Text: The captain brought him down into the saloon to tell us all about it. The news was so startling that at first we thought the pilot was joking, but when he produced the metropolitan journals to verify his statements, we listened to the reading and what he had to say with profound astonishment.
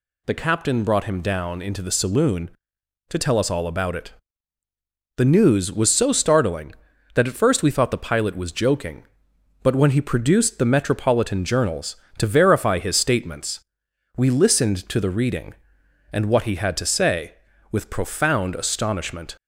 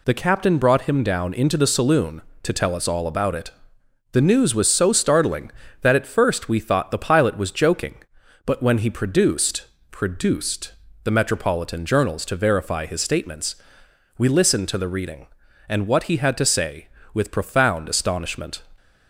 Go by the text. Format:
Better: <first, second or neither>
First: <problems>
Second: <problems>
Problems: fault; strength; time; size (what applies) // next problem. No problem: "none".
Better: first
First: none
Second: says "produced" twice; at 9.8 s